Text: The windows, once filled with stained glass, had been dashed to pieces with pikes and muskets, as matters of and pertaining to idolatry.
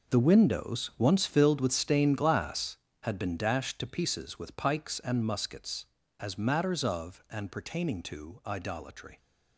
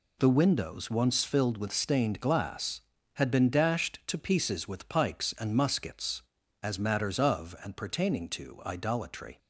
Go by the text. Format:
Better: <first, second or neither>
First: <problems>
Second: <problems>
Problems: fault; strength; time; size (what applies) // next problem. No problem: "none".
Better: second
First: gets quieter; strong; throughout; 12.5 dB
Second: none